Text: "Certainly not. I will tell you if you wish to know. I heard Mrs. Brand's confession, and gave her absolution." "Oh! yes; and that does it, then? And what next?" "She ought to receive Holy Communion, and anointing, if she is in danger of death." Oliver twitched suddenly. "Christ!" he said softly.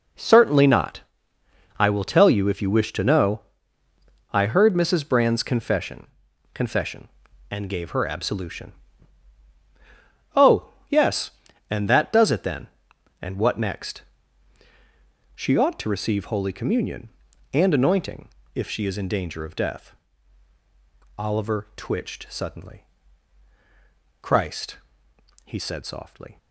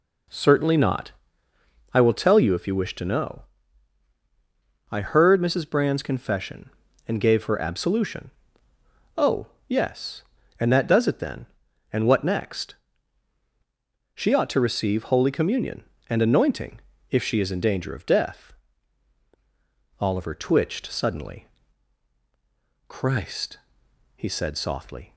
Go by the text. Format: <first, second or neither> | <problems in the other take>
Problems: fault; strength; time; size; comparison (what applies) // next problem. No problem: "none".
second | says "confession" twice; at 6.5 s